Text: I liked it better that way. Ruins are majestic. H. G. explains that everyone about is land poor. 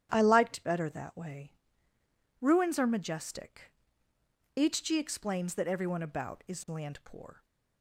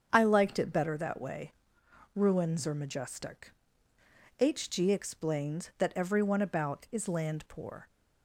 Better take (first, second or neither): second